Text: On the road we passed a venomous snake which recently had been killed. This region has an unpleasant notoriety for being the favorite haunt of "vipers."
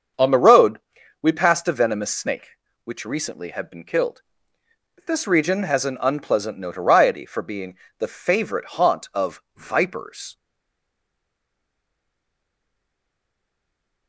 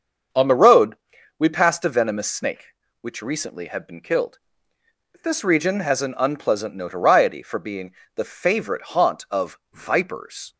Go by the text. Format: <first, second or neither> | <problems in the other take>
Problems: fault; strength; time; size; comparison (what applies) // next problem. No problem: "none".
second | starts louder than the rest; until 1.6 s; 7 dB; also in the second // pauses between "road" and "we"; at 0.7 s; 0.44 s long; also in the second // pauses between "being" and "the"; slight; at 7.7 s; 0.22 s long; slight in the second // stays silent after the last word; strong; from 10.3 s on; 3.7 s long